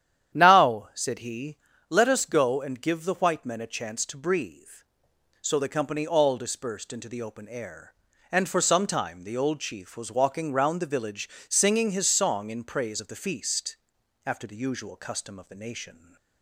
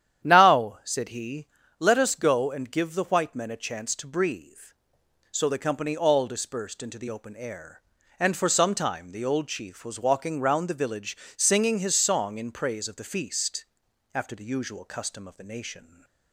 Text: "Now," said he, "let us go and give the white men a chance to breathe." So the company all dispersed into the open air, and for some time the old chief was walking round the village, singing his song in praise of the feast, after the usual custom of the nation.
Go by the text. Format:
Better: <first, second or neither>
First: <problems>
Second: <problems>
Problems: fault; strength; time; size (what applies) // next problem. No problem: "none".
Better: neither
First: starts louder than the rest; strong; until 1.4 s; 10 dB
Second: starts louder than the rest; strong; until 1.3 s; 10 dB